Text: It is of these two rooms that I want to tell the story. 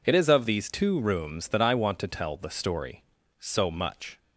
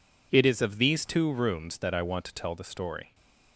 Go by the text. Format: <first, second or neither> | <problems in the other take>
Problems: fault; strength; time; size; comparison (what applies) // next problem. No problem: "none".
second | goes on to say "So much"; noticeable; from 3.3 s on; 0.80 s long